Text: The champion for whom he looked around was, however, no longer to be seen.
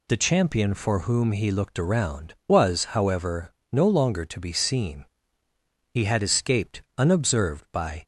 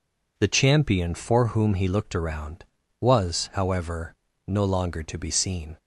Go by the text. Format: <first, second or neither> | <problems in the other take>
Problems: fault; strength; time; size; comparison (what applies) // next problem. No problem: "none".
second | goes on to say "He had escaped unobserved by"; strong; from 5.9 s on; 2.1 s long